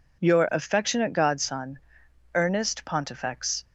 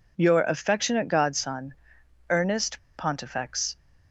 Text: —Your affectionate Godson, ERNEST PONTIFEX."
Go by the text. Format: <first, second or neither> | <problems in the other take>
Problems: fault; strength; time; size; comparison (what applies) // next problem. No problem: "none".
first | pauses between "ERNEST" and "PONTIFEX"; slight; at 2.7 s; 0.17 s long